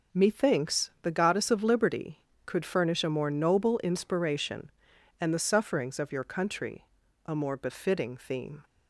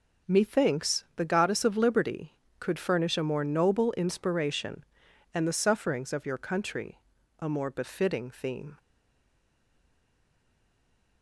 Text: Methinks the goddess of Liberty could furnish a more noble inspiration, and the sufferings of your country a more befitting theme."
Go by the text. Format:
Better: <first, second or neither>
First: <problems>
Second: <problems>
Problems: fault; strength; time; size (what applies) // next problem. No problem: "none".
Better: first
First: pauses between "country" and "a"; at 6.8 s; 0.42 s long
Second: pauses between "country" and "a"; at 6.9 s; 0.42 s long // stays silent after the last word; from 8.7 s on; 2.5 s long